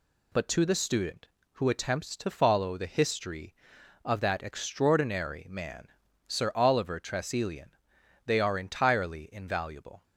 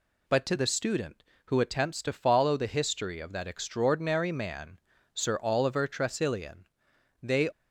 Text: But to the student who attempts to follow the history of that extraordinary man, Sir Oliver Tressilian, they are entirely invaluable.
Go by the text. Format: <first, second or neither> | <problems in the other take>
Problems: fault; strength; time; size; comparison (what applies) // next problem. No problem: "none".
first | stops before "are entirely invaluable"; at 7.5 s